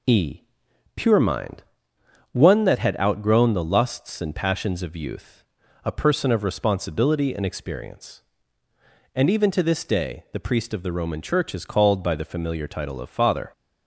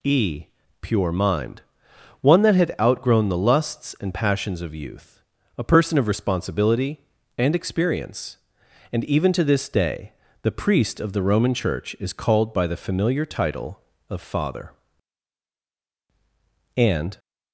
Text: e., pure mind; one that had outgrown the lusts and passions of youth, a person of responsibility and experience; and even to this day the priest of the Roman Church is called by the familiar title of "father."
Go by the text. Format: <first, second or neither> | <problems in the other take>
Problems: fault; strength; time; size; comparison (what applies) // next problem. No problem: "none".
first | pauses between "day" and "the"; slight; at 10.1 s; 0.28 s long // goes on to say "And"; slight; from 16.7 s on; 0.44 s long